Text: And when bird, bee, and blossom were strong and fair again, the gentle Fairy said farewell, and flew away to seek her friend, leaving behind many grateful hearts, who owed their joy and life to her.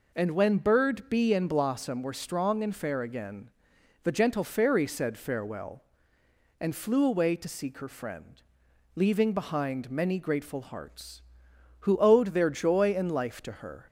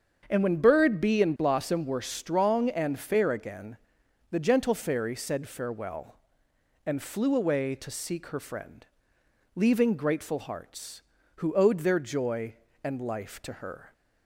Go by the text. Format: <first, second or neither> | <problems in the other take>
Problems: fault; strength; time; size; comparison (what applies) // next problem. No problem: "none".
first | starts louder than the rest; strong; until 1.3 s; 7 dB // skips "behind many"; at 9.9 s